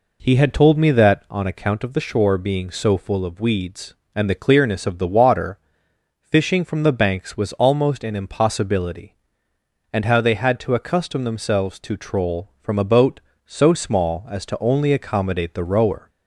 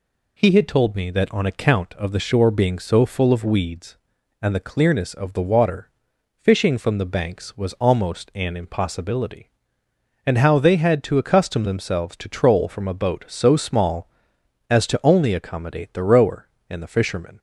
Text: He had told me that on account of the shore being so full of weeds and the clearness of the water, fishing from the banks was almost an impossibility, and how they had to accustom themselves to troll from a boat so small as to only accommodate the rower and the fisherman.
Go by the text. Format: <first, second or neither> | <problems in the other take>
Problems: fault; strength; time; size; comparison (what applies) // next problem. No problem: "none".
second | stops before "and the fisherman"; at 16.0 s